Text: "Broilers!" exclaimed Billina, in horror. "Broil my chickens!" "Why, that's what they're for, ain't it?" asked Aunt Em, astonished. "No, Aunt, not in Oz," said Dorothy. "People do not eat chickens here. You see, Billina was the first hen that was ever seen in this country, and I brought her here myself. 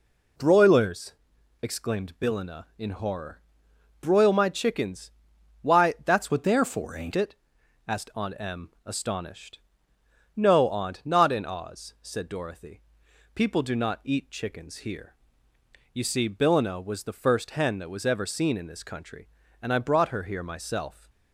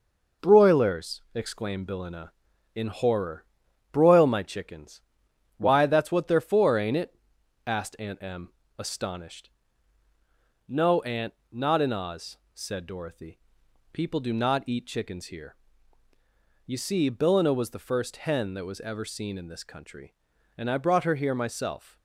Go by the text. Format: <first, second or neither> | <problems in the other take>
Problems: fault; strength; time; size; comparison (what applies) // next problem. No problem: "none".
second | changes voice from "what" to "ain't"; from 6.3 to 7.1 s; 0.8 s long